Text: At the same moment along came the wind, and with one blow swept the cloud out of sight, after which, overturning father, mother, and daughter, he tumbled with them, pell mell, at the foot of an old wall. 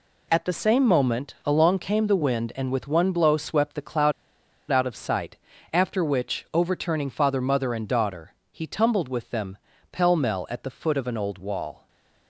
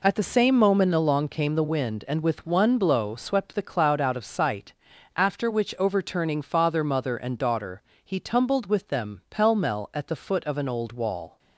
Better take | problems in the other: second | pauses between "cloud" and "out"; noticeable; at 4.1 s; 0.59 s long // stays silent after the last word; slight; from 11.7 s on; 0.5 s long

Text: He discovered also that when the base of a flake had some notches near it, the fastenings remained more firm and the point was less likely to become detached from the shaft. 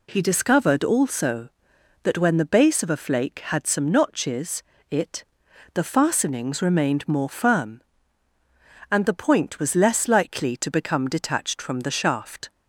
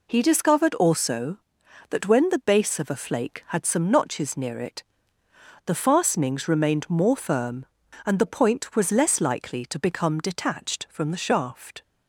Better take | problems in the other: second | skips "near"; at 4.7 s

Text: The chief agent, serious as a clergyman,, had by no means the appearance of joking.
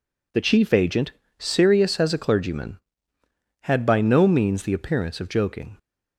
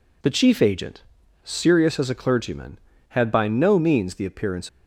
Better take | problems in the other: first | stops before "of joking"; at 4.6 s

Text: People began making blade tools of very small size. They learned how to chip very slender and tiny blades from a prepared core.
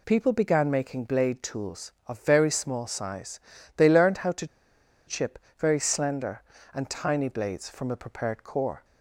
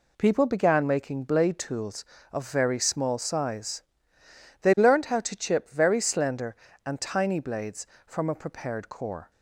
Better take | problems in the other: second | pauses between "to" and "chip"; noticeable; at 4.4 s; 0.62 s long // pauses between "chip" and "very"; slight; at 5.3 s; 0.20 s long

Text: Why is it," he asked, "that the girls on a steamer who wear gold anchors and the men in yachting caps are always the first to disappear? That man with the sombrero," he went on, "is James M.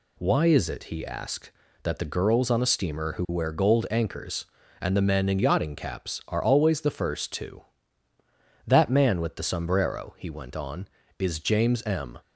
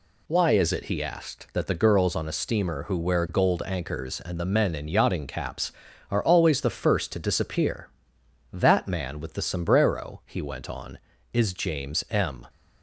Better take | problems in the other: second | skips "disappear"; at 8.1 s

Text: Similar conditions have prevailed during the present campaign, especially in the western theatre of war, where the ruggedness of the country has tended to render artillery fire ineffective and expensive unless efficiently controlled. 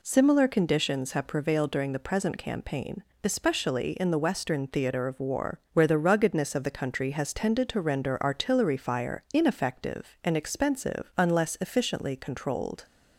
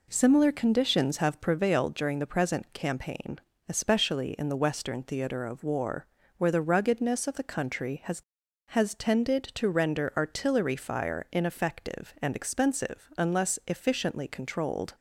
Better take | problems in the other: first | says "has" twice; at 8.6 s

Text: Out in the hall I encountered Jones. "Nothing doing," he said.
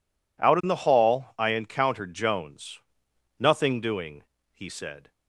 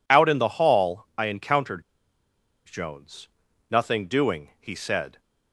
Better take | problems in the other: first | pauses between "encountered" and "Jones"; noticeable; at 1.8 s; 0.83 s long

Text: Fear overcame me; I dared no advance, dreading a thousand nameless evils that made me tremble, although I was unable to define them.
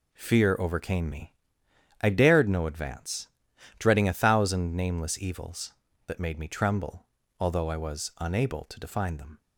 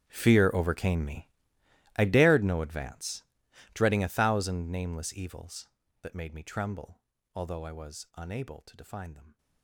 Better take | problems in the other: first | gets quieter; strong; throughout; 20 dB

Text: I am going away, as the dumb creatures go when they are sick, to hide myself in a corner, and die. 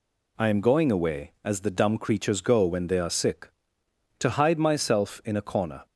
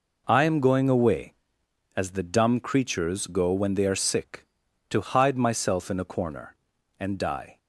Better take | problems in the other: second | stops before "and die"; at 5.8 s

